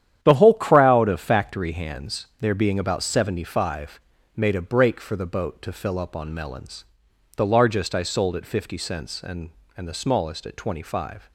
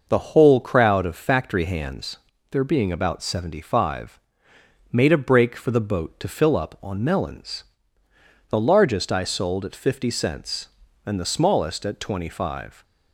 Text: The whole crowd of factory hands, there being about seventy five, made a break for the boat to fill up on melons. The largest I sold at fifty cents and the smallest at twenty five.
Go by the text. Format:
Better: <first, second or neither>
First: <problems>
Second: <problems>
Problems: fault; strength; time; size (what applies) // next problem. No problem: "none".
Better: second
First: starts louder than the rest; strong; until 1.2 s; 10 dB // says "and" twice; at 9.7 s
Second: none